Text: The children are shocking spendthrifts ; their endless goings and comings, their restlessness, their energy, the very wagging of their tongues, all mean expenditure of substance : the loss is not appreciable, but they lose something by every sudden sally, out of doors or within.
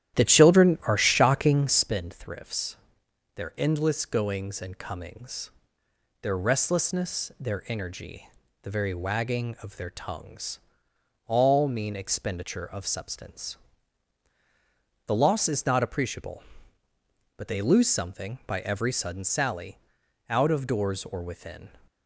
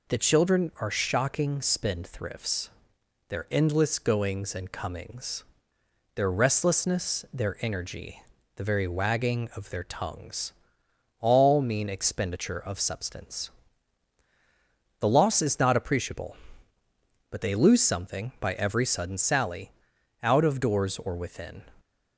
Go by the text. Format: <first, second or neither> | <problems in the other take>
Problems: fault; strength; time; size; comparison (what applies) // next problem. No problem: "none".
second | starts louder than the rest; strong; until 2.0 s; 12 dB